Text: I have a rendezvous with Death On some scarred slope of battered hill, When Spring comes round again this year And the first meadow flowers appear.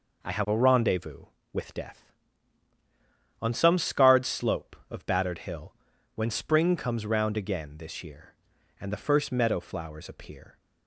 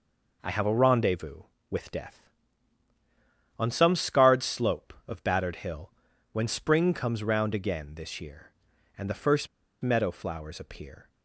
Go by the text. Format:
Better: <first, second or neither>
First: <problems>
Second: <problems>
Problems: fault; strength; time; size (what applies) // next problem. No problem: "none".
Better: first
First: none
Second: pauses between "first" and "meadow"; slight; at 9.4 s; 0.35 s long